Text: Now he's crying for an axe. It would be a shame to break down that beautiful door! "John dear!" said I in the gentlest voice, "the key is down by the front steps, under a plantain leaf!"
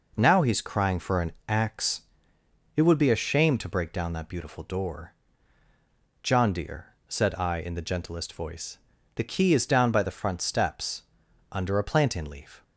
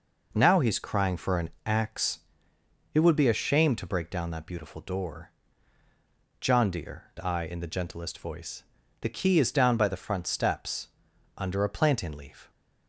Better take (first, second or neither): first